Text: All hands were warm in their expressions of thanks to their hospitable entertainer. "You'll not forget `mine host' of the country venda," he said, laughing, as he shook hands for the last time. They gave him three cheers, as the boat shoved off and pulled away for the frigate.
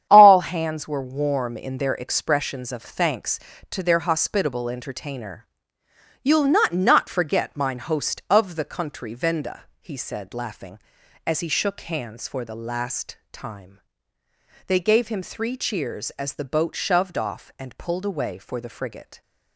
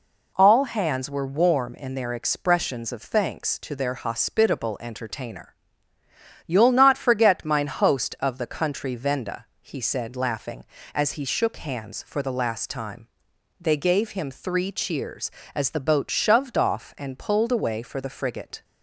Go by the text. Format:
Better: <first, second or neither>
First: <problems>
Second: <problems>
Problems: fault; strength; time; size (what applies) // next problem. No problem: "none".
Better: second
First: starts louder than the rest; strong; until 1.1 s; 9.5 dB // says "not" twice; at 6.7 s // pauses between "last" and "time"; slight; at 13.1 s; 0.16 s long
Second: none